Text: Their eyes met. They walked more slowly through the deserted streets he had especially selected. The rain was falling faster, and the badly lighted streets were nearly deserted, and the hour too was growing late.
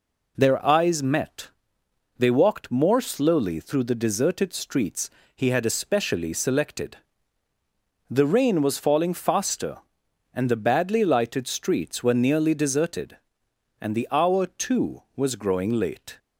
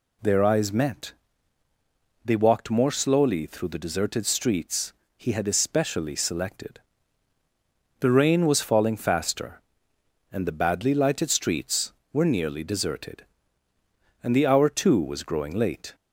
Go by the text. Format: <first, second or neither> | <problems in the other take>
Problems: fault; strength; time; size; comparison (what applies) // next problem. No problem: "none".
neither | pauses between "streets" and "he"; slight; the same in both